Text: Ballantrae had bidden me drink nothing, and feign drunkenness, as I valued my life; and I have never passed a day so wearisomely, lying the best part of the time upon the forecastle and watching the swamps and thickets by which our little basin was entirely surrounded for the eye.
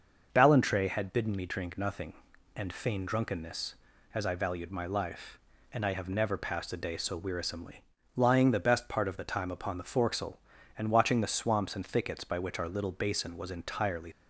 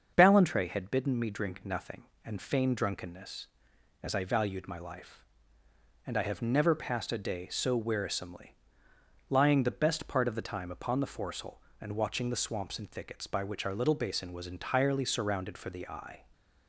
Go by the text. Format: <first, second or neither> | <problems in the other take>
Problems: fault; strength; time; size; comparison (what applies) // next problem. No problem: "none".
second | starts louder than the rest; until 1.3 s; 6 dB; also in the second // stops before "surrounded for the eye"; at 14.1 s